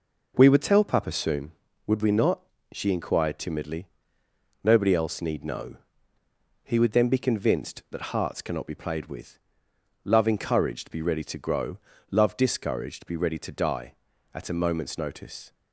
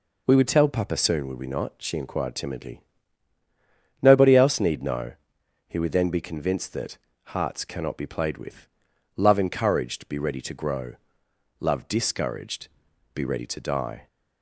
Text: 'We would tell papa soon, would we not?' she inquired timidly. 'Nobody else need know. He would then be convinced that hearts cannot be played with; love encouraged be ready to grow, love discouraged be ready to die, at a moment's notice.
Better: first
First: none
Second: pauses between "that" and "hearts"; slight; at 6.9 s; 0.28 s long // pauses between "discouraged" and "be"; at 12.6 s; 0.44 s long // stops before "at a moment's notice"; at 14.0 s

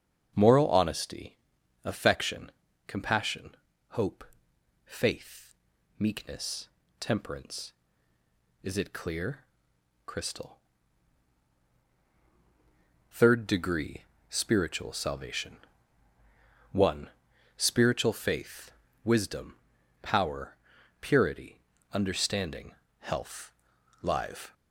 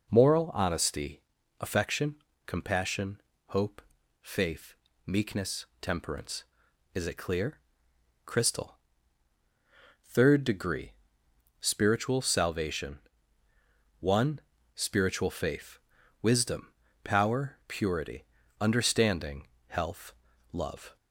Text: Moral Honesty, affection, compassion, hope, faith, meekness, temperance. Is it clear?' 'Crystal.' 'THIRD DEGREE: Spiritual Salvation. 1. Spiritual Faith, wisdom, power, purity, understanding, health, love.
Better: second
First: starts louder than the rest; strong; until 1.3 s; 7.5 dB // says "live" for "love"; at 24.0 s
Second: none

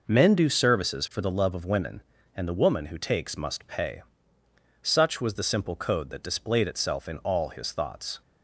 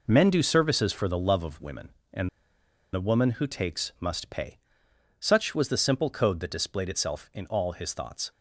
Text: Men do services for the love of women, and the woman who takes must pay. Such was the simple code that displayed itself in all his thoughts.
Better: first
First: none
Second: pauses between "and" and "the"; noticeable; at 2.2 s; 0.65 s long

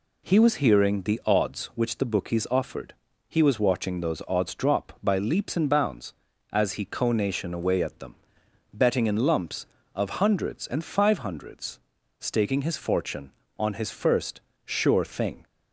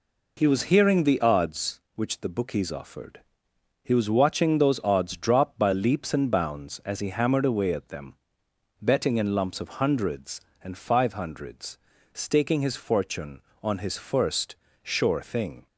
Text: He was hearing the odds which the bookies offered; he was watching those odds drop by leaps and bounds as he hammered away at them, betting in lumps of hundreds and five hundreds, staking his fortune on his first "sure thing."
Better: second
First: says "conation" for "hammered"; at 6.8 s // pauses between "first" and "sure"; slight; at 14.3 s; 0.26 s long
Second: pauses between "first" and "sure"; slight; at 14.5 s; 0.26 s long

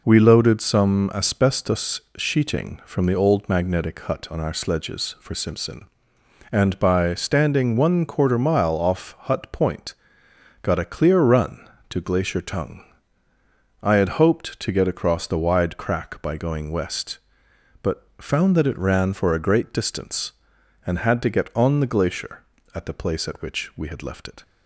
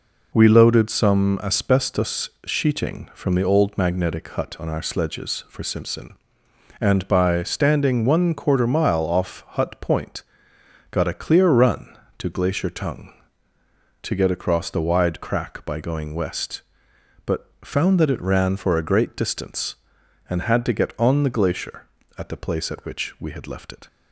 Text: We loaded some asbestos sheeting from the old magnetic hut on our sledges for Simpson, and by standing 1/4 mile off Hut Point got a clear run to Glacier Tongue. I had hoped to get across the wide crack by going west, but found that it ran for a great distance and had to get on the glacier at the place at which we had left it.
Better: first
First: pauses between "asbestos" and "sheeting"; slight; at 2.0 s; 0.16 s long // pauses between "Point" and "got"; noticeable; at 9.9 s; 0.68 s long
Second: pauses between "asbestos" and "sheeting"; slight; at 2.3 s; 0.16 s long // pauses between "Point" and "got"; noticeable; at 10.2 s; 0.68 s long // skips "I had hoped"; at 13.5 s

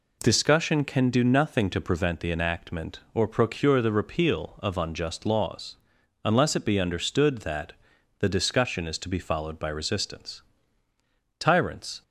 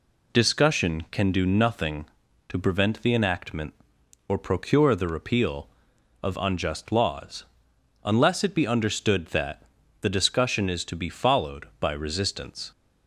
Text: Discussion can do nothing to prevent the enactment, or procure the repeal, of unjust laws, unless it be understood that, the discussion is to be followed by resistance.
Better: second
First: goes on to say "Tyrants"; noticeable; from 11.3 s on; 0.64 s long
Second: none

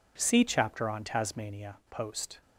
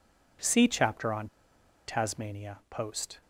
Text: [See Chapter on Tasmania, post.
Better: first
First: none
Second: pauses between "on" and "Tasmania"; noticeable; at 1.2 s; 0.59 s long

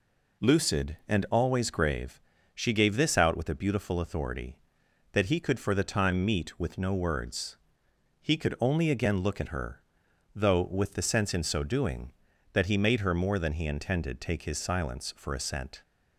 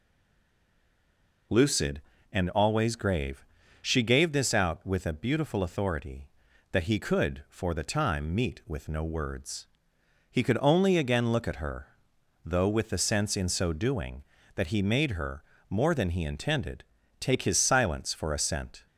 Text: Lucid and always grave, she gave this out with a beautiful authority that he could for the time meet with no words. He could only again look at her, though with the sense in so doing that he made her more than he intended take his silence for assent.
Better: first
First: none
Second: stays silent before the first word; noticeable; until 1.5 s; 1.5 s long // pauses between "her" and "more"; slight; at 15.4 s; 0.26 s long // pauses between "intended" and "take"; at 16.8 s; 0.38 s long

